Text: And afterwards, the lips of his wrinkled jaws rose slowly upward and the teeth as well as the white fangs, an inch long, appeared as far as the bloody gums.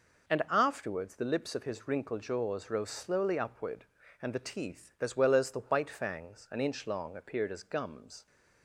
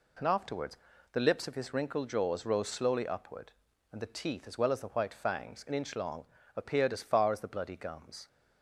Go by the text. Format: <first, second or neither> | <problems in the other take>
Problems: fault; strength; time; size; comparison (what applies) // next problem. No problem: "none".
second | skips "far as the bloody"; at 7.6 s